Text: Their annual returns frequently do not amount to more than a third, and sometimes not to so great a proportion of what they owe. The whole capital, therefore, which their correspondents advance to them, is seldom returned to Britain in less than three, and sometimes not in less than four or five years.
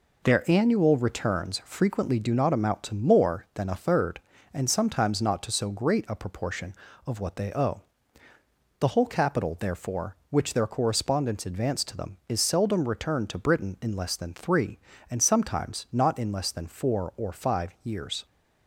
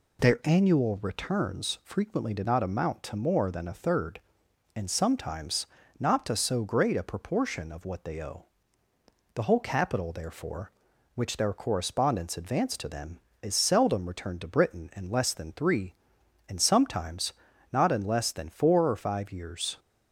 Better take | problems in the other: first | says "did" for "do"; at 2.3 s // pauses between "sometimes" and "not"; slight; at 5.6 s; 0.32 s long // pauses between "sometimes" and "not"; at 17.3 s; 0.40 s long

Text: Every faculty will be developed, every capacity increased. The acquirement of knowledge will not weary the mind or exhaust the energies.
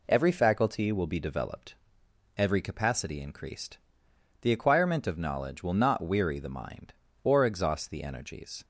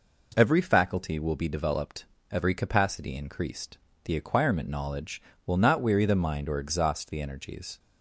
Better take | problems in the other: first | skips "of"; at 4.6 s

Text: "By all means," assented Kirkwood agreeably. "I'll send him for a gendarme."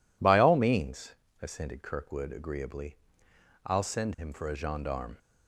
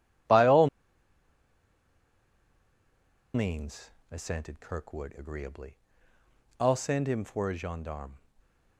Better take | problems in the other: first | pauses between "all" and "means"; strong; at 0.6 s; 2.6 s long

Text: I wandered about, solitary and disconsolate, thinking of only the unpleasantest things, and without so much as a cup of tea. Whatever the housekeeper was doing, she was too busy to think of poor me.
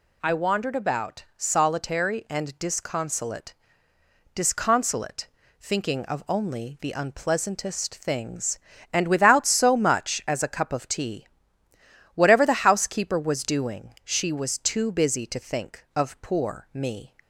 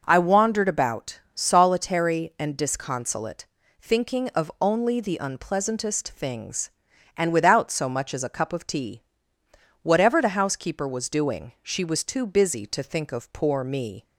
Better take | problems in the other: second | says "disconsolate" twice; at 4.3 s

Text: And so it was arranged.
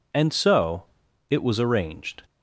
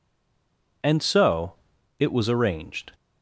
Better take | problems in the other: first | stays silent before the first word; slight; until 0.8 s; 0.8 s long // pauses between "so" and "it"; noticeable; at 1.5 s; 0.46 s long; noticeable in the first

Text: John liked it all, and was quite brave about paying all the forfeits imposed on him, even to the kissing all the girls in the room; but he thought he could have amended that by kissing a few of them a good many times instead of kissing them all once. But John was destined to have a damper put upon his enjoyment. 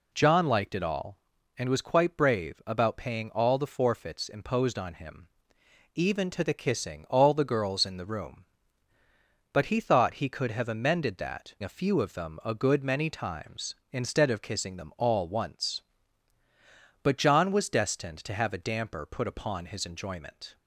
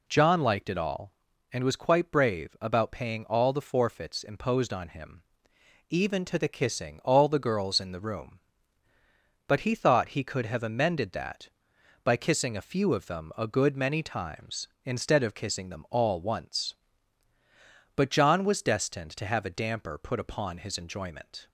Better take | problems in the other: second | skips "by kissing"; at 11.5 s

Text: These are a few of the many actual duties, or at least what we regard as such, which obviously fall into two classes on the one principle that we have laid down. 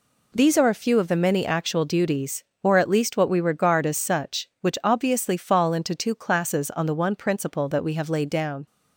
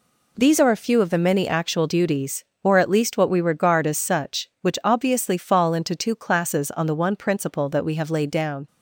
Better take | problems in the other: neither | none

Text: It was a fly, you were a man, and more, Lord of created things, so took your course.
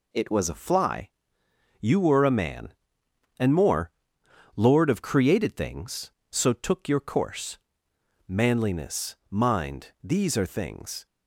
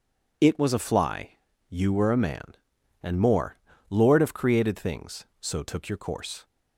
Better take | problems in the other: second | goes on to say "Manliness mind these are things"; strong; from 8.2 s on; 2.7 s long

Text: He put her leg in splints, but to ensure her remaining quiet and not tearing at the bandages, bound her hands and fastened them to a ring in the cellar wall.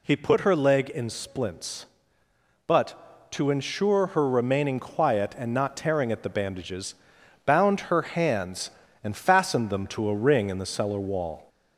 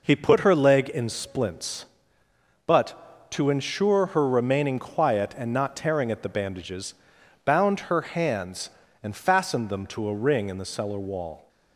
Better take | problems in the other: second | gets louder; slight; throughout; 2 dB

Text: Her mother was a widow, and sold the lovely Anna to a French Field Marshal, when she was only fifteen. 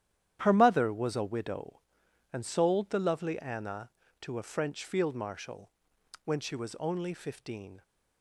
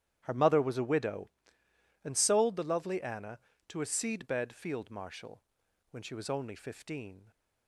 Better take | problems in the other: first | starts louder than the rest; strong; until 1.2 s; 10.5 dB; strong in the first // says "Seedbed" for "French"; at 3.8 s

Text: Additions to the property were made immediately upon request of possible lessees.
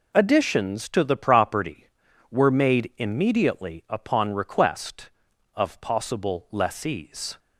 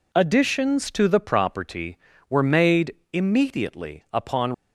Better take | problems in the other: first | pauses between "made" and "immediately"; slight; at 2.9 s; 0.20 s long // stops before "request of possible lessees"; at 4.5 s

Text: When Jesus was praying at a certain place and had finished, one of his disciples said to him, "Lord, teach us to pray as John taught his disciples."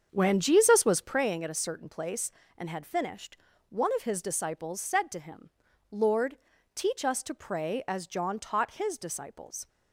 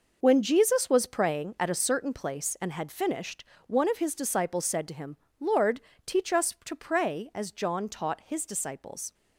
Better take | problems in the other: second | starts louder than the rest; strong; until 1.3 s; 7 dB

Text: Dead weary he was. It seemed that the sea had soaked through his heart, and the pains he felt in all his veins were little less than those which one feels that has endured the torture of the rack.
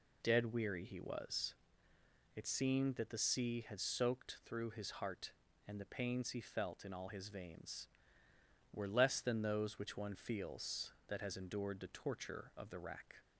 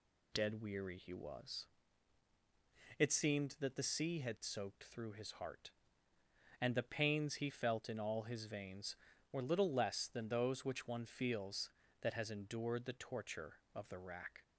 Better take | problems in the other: second | skips "little"; at 8.8 s

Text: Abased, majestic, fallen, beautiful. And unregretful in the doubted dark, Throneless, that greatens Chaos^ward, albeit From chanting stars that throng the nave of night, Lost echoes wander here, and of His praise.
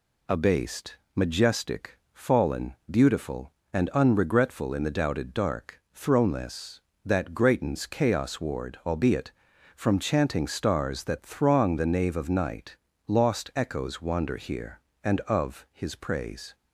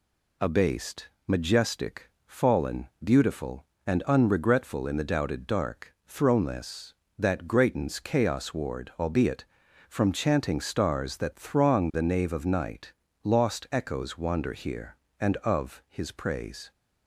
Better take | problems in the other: neither | none

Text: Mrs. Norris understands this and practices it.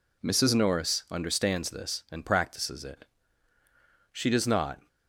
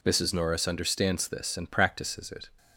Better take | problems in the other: second | goes on to say "She does not"; noticeable; from 4.1 s on; 0.76 s long

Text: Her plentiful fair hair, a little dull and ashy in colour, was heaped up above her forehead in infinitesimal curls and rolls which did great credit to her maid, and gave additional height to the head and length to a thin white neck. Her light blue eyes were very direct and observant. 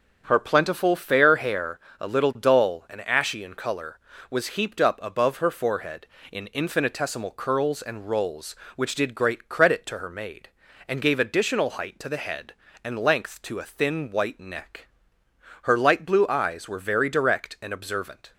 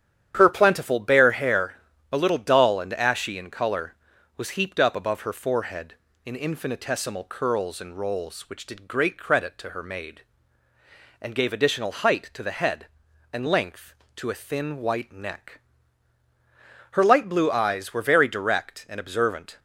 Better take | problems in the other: first | starts louder than the rest; strong; until 1.3 s; 9.5 dB; also in the first // says "bare" for "fair"; at 0.9 s

